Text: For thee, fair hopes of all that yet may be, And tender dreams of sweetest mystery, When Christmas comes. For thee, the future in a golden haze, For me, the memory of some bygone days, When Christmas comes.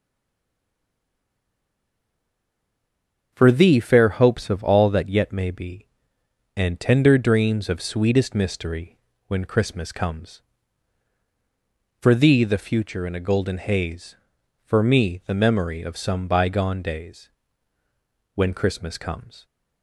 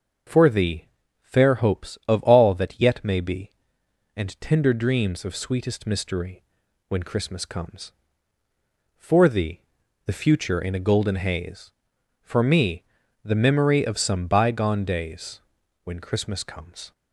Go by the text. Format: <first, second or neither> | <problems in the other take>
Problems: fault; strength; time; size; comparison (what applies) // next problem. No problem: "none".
second | stays silent before the first word; strong; until 3.3 s; 3.3 s long // starts louder than the rest; until 4.3 s; 7 dB; noticeable in the second